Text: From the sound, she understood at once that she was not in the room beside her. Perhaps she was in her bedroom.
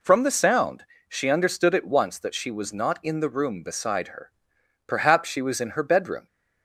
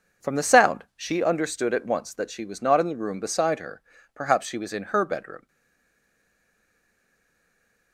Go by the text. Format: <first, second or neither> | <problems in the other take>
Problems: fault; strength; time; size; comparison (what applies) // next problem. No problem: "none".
first | stays silent after the last word; strong; from 5.4 s on; 2.5 s long